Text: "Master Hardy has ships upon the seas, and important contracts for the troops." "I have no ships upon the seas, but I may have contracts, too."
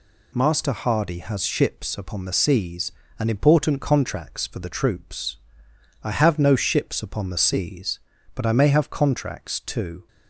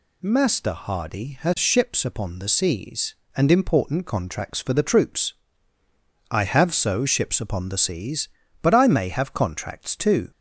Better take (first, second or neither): first